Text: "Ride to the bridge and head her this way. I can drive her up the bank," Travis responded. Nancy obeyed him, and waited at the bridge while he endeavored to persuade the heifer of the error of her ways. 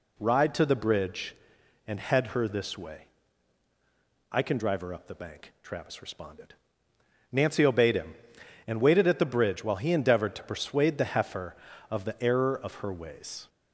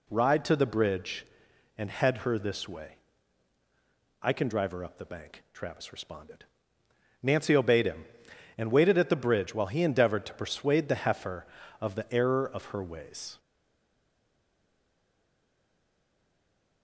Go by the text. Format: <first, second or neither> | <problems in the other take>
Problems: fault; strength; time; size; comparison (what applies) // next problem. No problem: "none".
first | stays silent after the last word; strong; from 13.3 s on; 3.5 s long